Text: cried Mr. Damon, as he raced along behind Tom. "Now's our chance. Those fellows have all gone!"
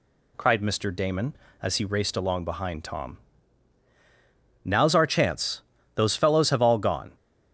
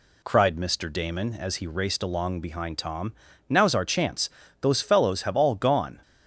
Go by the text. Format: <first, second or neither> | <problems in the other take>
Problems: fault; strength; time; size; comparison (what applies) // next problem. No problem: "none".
neither | none